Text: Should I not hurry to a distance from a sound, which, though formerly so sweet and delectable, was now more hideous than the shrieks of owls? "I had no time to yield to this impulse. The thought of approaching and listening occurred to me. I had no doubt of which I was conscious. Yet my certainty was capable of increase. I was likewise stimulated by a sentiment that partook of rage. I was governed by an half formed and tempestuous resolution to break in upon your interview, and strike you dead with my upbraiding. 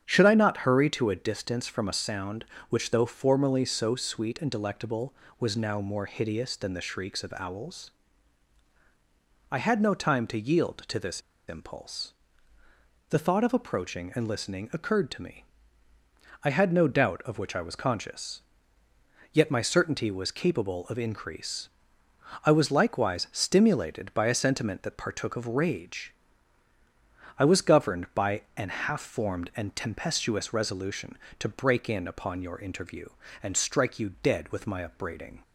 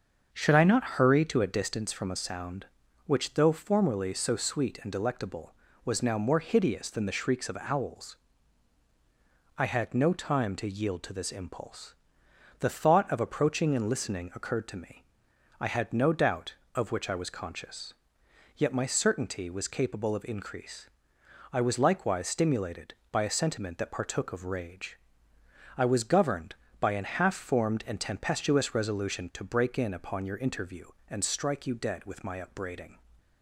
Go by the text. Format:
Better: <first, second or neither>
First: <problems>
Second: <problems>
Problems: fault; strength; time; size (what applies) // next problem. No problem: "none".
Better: second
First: starts louder than the rest; strong; until 1.0 s; 8 dB // pauses between "this" and "impulse"; slight; at 11.2 s; 0.27 s long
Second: starts louder than the rest; until 1.3 s; 6.5 dB